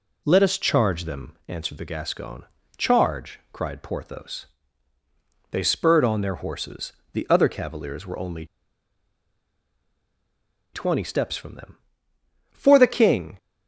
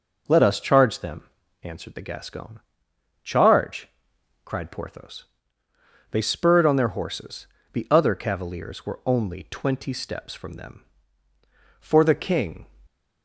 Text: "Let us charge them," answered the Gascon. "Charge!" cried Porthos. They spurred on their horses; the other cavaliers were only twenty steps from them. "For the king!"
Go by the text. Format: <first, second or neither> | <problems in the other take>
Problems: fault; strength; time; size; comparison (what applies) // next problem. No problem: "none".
second | pauses between "only" and "twenty"; strong; at 8.4 s; 2.2 s long